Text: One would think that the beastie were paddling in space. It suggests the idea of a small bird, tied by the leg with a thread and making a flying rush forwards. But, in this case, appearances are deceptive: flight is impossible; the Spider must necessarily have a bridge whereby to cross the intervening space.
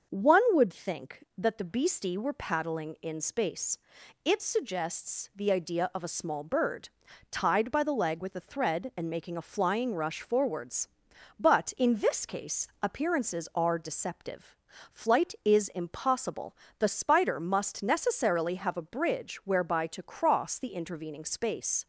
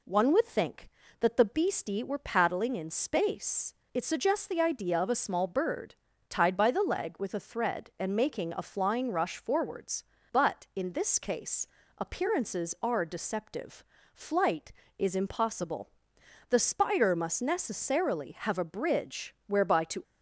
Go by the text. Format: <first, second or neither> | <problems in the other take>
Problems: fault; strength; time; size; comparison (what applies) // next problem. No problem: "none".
first | stops before "cross the intervening space"; at 20.0 s